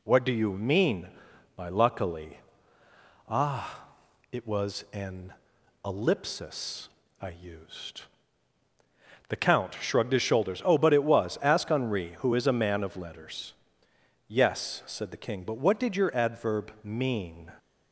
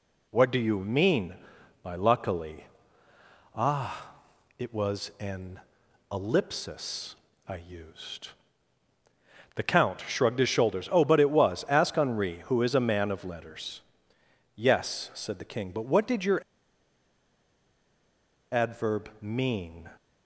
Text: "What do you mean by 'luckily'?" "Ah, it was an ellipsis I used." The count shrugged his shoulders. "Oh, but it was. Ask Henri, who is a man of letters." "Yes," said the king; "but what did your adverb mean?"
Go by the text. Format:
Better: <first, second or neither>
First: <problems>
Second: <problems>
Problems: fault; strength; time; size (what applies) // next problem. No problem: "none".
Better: first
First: pauses between "an" and "ellipsis"; noticeable; at 5.3 s; 0.52 s long // pauses between "ellipsis" and "I"; slight; at 6.8 s; 0.32 s long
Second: pauses between "an" and "ellipsis"; noticeable; at 5.5 s; 0.52 s long // pauses between "ellipsis" and "I"; slight; at 7.1 s; 0.32 s long // pauses between "your" and "adverb"; strong; at 16.4 s; 2.0 s long